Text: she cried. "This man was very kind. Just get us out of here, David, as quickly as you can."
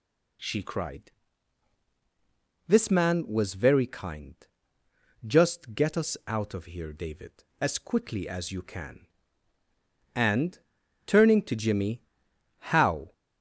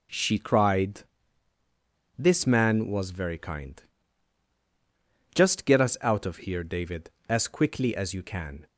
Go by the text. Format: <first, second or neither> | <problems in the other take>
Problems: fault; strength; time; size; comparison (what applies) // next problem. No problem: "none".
second | goes on to say "And turning to Jimmy How"; strong; from 10.1 s on; 2.9 s long